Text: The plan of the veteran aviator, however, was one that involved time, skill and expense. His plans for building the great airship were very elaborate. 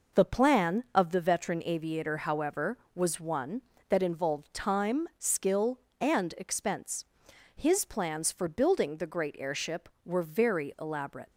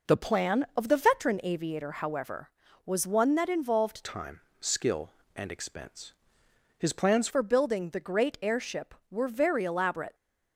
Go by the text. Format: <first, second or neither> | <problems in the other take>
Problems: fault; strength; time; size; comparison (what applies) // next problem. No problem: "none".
first | changes voice from "time" to "plans"; from 4.0 to 7.2 s; 3.2 s long